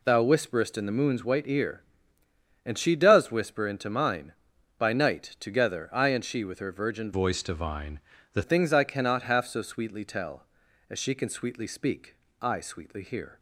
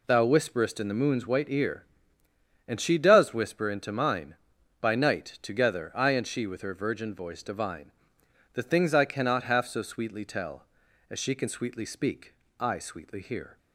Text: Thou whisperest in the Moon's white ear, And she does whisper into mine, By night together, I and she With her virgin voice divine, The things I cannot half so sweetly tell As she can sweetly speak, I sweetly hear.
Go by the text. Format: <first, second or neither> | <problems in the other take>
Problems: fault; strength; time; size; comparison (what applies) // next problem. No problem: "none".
second | changes voice from "voice" to "The"; from 7.1 to 8.4 s; 1.3 s long